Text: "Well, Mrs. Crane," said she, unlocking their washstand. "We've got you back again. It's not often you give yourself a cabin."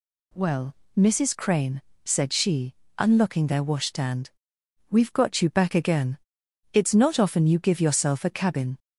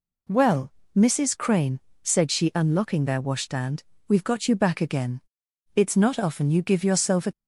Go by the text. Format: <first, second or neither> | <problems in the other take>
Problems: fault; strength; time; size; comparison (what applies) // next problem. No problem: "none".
first | stops before "cabin"; at 7.3 s